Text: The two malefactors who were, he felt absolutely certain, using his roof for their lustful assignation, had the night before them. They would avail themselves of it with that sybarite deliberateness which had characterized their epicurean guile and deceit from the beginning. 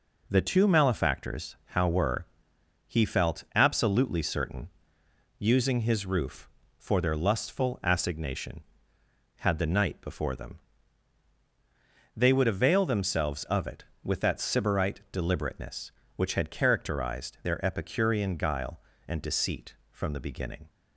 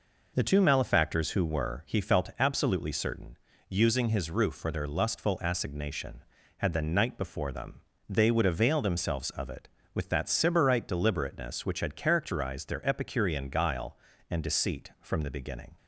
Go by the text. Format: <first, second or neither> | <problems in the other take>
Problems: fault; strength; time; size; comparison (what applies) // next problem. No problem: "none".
second | says "how" for "who"; at 1.6 s